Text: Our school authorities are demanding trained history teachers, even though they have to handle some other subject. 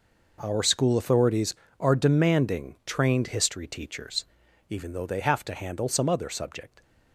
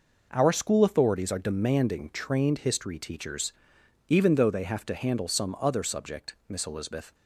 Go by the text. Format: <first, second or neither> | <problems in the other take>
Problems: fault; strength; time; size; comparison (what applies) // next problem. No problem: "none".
first | goes on to say "Miss Elizabeth"; noticeable; from 6.4 s on; 0.66 s long